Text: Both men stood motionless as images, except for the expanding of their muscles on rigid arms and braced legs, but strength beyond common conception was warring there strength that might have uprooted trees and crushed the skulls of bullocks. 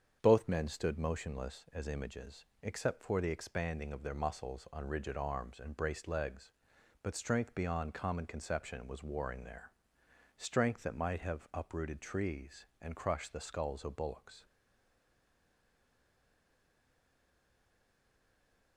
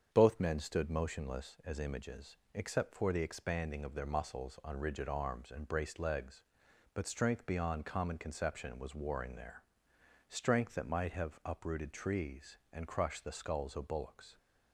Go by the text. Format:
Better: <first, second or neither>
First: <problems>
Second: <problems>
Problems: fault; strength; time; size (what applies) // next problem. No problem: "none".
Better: second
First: starts louder than the rest; strong; until 1.2 s; 7.5 dB // pauses between "there" and "strength"; noticeable; at 9.7 s; 0.70 s long // stays silent after the last word; strong; from 14.4 s on; 4.3 s long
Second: starts louder than the rest; strong; until 1.1 s; 7.5 dB // pauses between "there" and "strength"; noticeable; at 9.6 s; 0.70 s long